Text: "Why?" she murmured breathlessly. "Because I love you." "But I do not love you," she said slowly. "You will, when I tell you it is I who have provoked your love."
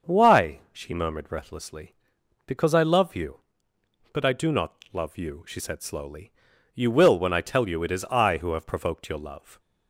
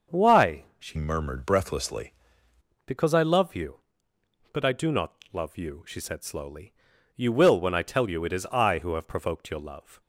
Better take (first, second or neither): first